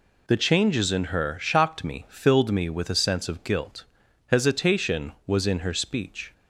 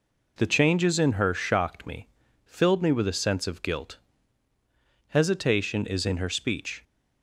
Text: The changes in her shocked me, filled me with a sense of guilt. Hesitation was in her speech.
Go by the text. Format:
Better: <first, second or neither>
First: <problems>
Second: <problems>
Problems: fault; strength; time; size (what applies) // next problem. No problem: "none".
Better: first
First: none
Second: says "is" for "was"; at 5.8 s